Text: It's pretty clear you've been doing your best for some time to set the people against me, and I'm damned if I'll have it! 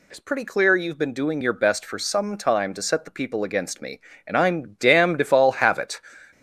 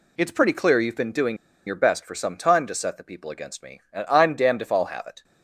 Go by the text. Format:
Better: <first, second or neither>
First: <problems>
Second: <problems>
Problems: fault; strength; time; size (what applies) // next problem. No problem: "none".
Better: first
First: none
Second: pauses between "doing" and "your"; slight; at 1.3 s; 0.30 s long